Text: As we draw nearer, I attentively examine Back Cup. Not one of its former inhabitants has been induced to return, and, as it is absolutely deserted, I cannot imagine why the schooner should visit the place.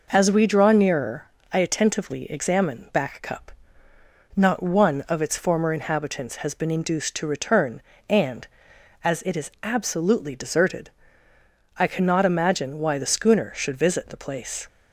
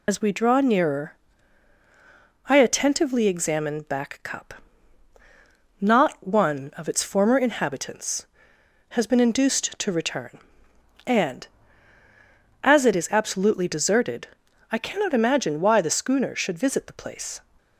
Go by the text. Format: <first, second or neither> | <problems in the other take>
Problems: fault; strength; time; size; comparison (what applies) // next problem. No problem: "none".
first | loses the start of "As"; at 0.0 s; 65 ms